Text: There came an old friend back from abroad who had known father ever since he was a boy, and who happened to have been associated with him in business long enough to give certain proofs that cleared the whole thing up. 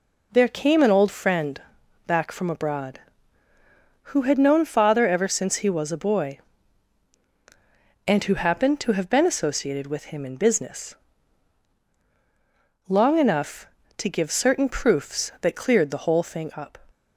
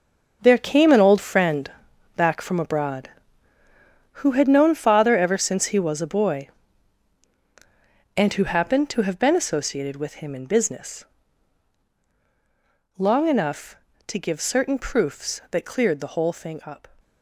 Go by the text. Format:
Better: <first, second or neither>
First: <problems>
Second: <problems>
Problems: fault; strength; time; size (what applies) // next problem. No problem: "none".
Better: first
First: pauses between "friend" and "back"; noticeable; at 1.5 s; 0.46 s long // pauses between "business" and "long"; strong; at 10.9 s; 1.9 s long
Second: gets quieter; strong; throughout; 10.5 dB // pauses between "friend" and "back"; noticeable; at 1.6 s; 0.46 s long // pauses between "business" and "long"; strong; at 11.0 s; 1.9 s long